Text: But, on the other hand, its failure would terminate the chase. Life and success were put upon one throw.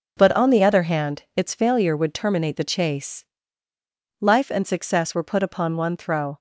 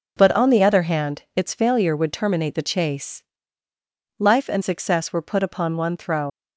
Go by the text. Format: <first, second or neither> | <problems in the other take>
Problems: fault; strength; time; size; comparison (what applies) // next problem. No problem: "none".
first | leaves "throw" unfinished; at 6.2 s; 85 ms